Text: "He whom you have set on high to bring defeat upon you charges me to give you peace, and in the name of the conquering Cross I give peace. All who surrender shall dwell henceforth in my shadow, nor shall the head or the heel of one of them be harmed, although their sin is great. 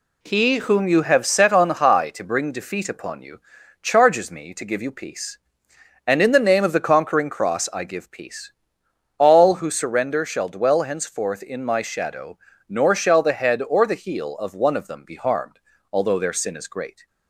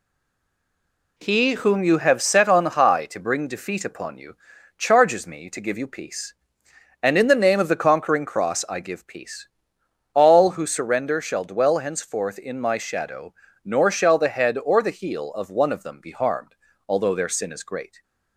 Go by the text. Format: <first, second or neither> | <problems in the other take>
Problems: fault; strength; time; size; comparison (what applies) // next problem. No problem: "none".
first | stays silent before the first word; noticeable; until 1.1 s; 1.1 s long // pauses between "you" and "charges"; at 4.3 s; 0.40 s long; also in the first